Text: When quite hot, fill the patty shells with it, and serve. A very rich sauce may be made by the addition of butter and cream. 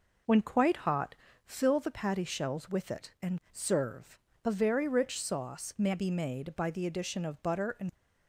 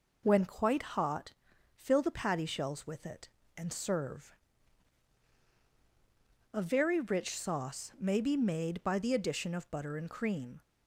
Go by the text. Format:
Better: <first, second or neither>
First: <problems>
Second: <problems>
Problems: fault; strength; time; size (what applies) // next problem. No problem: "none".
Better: second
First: stops before "cream"; at 7.9 s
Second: none